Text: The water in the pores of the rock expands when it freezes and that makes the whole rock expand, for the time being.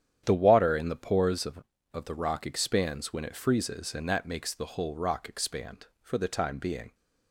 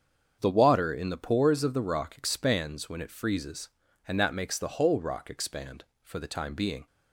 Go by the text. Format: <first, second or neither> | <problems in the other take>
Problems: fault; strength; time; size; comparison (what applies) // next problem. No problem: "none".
second | starts louder than the rest; strong; until 1.2 s; 9.5 dB; strong in the second // says "of" twice; at 1.9 s